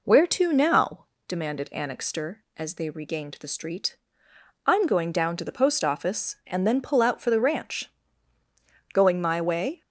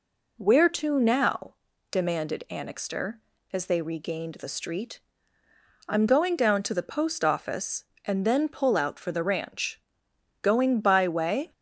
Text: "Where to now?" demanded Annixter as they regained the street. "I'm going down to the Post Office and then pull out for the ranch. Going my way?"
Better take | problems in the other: first | says "by" for "my"; at 10.8 s

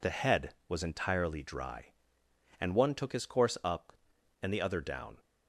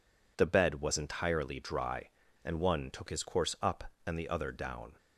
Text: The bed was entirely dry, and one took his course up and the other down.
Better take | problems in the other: second | says "head" for "bed"; at 0.1 s

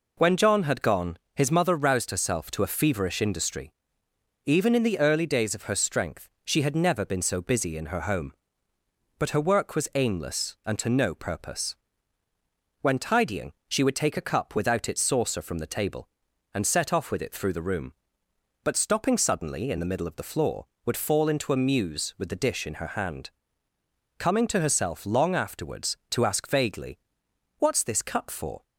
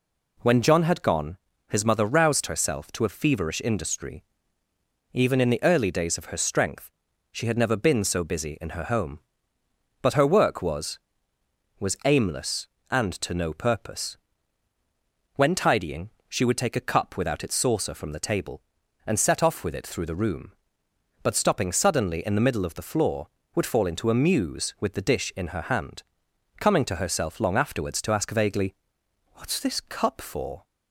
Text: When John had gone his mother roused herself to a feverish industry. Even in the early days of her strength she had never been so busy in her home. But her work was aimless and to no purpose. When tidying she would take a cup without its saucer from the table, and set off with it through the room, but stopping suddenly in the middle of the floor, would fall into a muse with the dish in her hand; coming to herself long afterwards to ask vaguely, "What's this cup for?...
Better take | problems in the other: first | pauses between "gone" and "his"; slight; at 1.3 s; 0.34 s long; slight in the first // pauses between "strength" and "she"; at 6.9 s; 0.40 s long; slight in the first // says "was" twice; at 11.7 s // pauses between "tidying" and "she"; slight; at 16.1 s; 0.18 s long; slight in the first

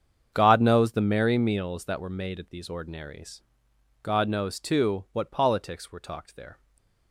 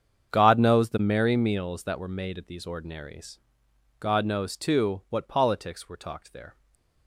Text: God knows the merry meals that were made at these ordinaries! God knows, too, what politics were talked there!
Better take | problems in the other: neither | starts louder than the rest; strong; the same in both // stays silent after the last word; slight; the same in both

